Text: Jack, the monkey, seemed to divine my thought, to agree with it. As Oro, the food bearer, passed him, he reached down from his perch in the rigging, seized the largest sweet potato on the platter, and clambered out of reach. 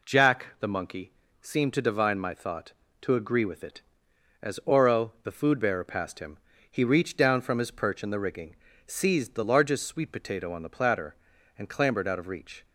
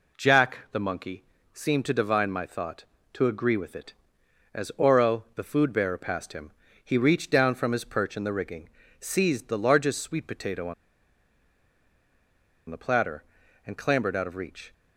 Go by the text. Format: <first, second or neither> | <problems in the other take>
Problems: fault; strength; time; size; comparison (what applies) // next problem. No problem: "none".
first | pauses between "on" and "the"; strong; at 10.7 s; 1.9 s long